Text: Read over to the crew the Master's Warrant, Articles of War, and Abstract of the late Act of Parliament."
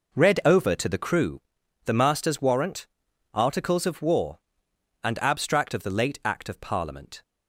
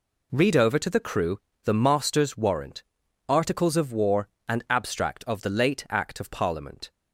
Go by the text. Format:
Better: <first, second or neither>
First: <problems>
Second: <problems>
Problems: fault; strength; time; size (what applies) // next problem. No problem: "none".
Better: second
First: starts louder than the rest; noticeable; until 1.2 s; 5 dB // pauses between "crew" and "the"; noticeable; at 1.3 s; 0.46 s long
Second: pauses between "crew" and "the"; slight; at 1.3 s; 0.26 s long